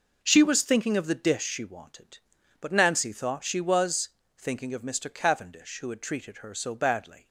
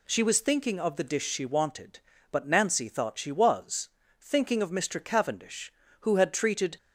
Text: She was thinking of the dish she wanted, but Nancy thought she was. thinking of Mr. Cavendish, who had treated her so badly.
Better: first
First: none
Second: stops before "her so badly"; at 6.7 s

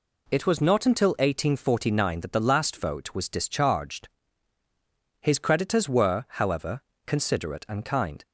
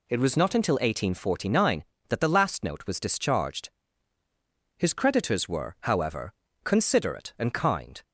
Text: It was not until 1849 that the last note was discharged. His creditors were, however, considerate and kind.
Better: second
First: says "vote" for "note"; at 2.7 s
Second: none

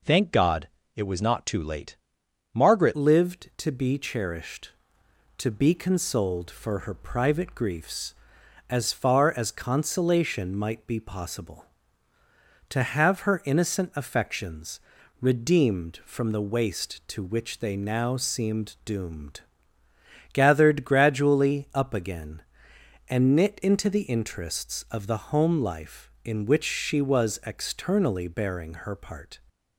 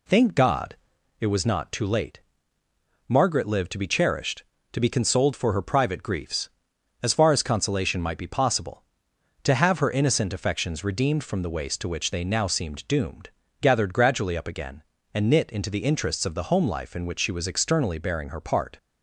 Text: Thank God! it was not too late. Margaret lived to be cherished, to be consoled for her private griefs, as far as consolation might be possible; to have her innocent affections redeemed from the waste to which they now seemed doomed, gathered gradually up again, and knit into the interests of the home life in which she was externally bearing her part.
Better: second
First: changes voice at "lived"; from 2.9 s on; 26.4 s long // pauses between "affections" and "redeemed"; at 14.7 s; 0.40 s long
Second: none

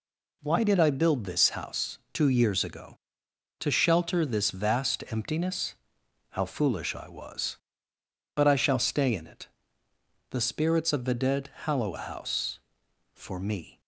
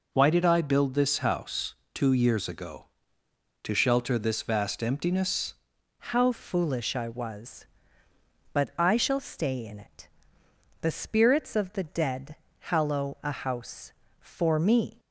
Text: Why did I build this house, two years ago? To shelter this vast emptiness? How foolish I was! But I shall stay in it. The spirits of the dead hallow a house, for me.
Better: first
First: none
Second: changes voice at "How"; from 6.1 s on; 8.8 s long // pauses between "dead" and "hallow"; slight; at 12.3 s; 0.24 s long

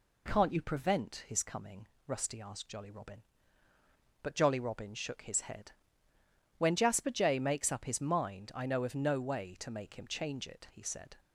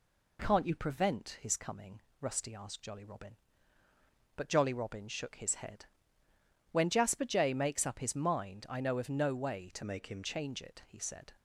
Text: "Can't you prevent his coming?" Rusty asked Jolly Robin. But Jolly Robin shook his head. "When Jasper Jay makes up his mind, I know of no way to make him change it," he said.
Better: first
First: none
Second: changes voice from "make" to "him"; from 9.8 to 10.2 s; 0.4 s long

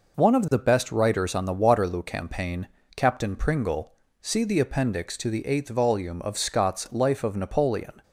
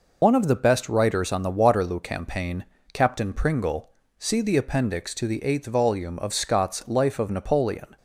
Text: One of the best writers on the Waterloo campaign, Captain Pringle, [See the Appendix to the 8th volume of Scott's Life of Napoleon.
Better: first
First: none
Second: loses the start of "One"; at 0.2 s; 65 ms

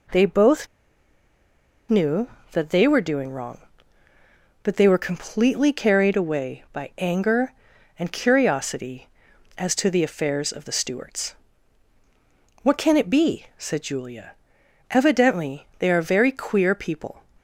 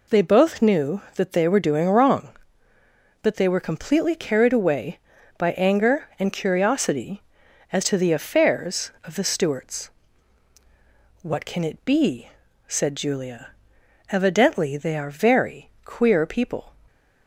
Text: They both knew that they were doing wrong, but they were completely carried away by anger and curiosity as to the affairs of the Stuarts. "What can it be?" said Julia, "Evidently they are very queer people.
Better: second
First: pauses between "both" and "knew"; at 0.6 s; 1.2 s long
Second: none

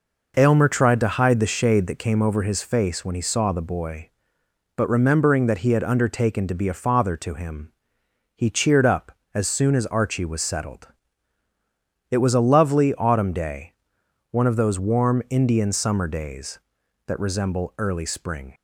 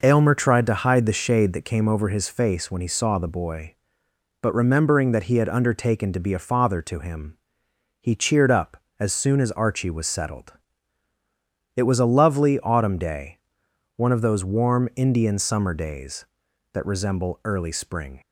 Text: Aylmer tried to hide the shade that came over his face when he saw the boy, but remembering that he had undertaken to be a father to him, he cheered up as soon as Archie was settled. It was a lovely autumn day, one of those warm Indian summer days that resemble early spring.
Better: neither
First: none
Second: none

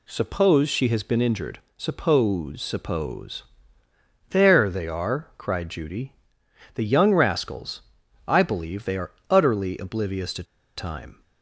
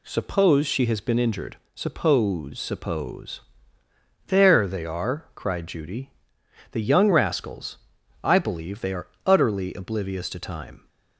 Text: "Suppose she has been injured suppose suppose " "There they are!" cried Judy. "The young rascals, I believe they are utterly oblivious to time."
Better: second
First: pauses between "injured" and "suppose"; slight; at 1.5 s; 0.18 s long // pauses between "are" and "utterly"; slight; at 9.1 s; 0.18 s long // pauses between "to" and "time"; slight; at 10.4 s; 0.32 s long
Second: pauses between "injured" and "suppose"; slight; at 1.5 s; 0.18 s long // pauses between "are" and "utterly"; slight; at 9.0 s; 0.18 s long

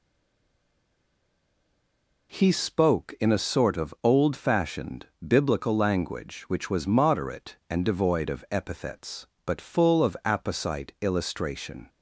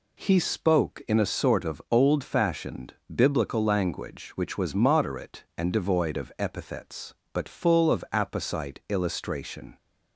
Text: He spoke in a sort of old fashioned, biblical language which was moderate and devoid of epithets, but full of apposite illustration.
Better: second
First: stays silent before the first word; until 2.3 s; 2.3 s long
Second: none

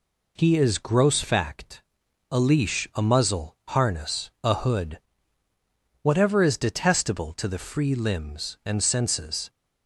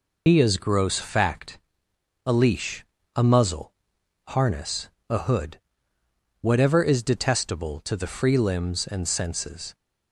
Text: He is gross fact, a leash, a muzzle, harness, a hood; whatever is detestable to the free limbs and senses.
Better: first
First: none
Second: loses the start of "He"; at 0.2 s; 40 ms

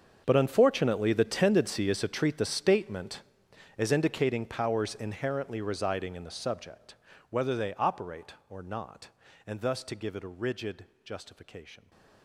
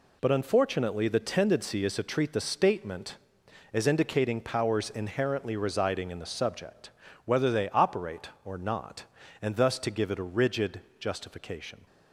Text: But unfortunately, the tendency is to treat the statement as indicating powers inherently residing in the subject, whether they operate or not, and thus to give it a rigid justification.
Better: second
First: gets quieter; strong; throughout; 18 dB // pauses between "rigid" and "justification"; slight; at 10.8 s; 0.18 s long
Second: pauses between "rigid" and "justification"; slight; at 10.8 s; 0.18 s long

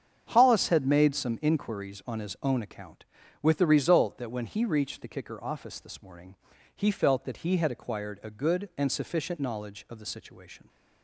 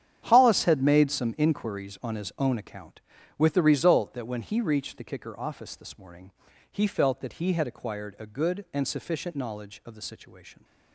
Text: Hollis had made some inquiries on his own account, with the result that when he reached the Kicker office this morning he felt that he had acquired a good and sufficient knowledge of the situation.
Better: first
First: starts louder than the rest; strong; until 1.3 s; 8 dB // pauses between "morning" and "he"; at 6.3 s; 0.40 s long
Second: gets quieter; strong; throughout; 13.5 dB // starts louder than the rest; strong; until 1.2 s; 9.5 dB // pauses between "morning" and "he"; at 6.3 s; 0.40 s long

